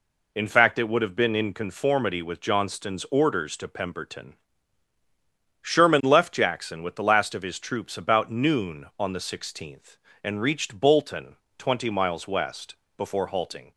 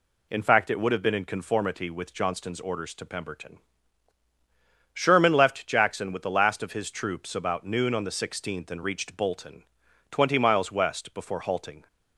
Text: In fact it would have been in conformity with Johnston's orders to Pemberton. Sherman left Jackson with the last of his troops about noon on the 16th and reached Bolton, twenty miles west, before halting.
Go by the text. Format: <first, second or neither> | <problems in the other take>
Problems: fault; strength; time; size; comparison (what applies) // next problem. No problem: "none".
neither | none